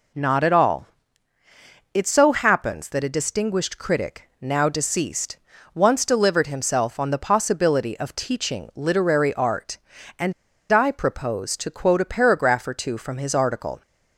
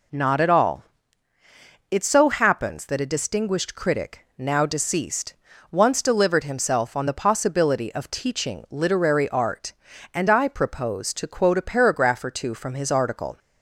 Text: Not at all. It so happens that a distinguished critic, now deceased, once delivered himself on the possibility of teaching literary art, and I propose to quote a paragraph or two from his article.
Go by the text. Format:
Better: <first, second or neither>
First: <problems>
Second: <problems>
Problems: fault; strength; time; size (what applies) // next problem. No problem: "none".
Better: second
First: pauses between "and" and "I"; at 10.3 s; 0.38 s long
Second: none